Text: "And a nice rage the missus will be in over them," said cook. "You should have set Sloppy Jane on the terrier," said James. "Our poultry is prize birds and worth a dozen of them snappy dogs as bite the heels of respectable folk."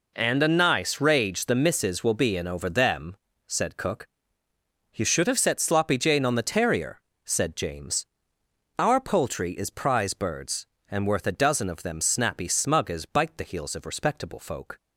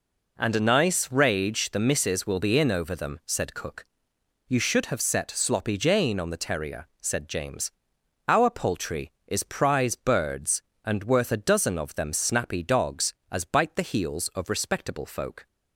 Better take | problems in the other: second | says "smug" for "dogs"; at 12.4 s

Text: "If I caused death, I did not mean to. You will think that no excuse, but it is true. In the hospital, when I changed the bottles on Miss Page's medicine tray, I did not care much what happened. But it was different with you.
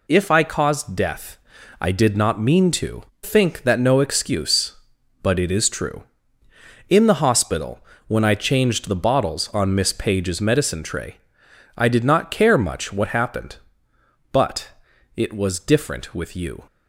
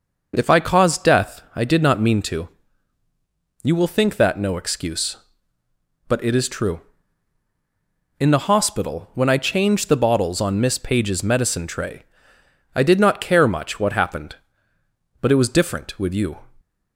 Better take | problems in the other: second | skips "You will"; at 3.1 s // pauses between "But" and "it"; noticeable; at 14.6 s; 0.48 s long

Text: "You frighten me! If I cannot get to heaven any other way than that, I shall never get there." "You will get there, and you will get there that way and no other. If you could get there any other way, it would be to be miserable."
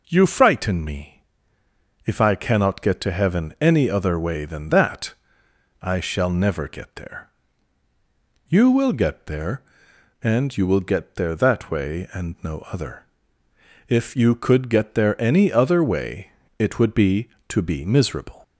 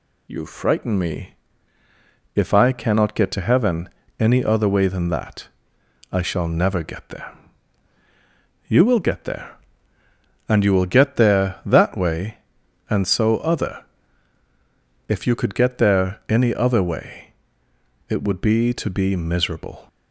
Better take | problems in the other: first | pauses between "heaven" and "any"; slight; at 3.8 s; 0.32 s long // says "so" for "no"; at 13.0 s

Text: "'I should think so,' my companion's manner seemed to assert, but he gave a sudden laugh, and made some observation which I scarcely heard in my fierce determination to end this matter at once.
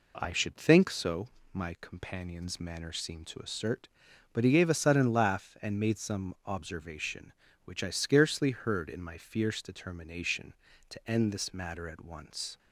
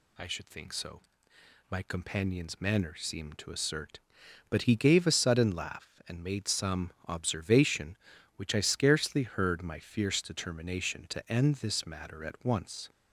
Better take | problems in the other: first | pauses between "some" and "observation"; slight; at 6.9 s; 0.16 s long // skips "in"; at 9.6 s

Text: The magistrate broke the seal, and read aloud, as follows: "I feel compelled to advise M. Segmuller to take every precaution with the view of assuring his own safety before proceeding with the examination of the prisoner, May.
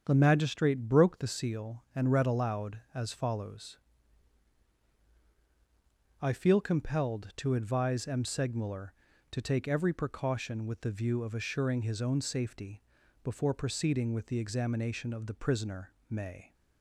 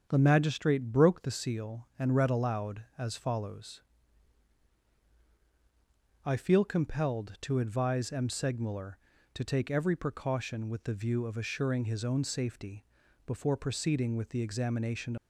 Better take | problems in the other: first | starts louder than the rest; strong; until 1.1 s; 7.5 dB; strong in the first // pauses between "safety" and "before"; at 12.8 s; 0.42 s long; also in the first // stops before "of the prisoner May"; at 15.1 s

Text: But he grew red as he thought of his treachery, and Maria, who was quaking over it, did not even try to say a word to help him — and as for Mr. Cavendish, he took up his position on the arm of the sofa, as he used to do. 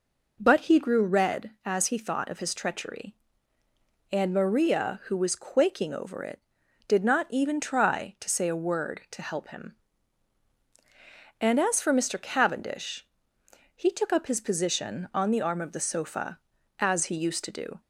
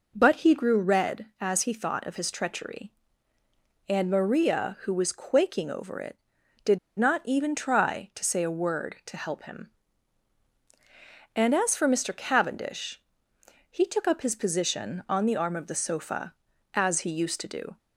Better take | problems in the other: first | pauses between "did" and "not"; slight; at 6.7 s; 0.19 s long

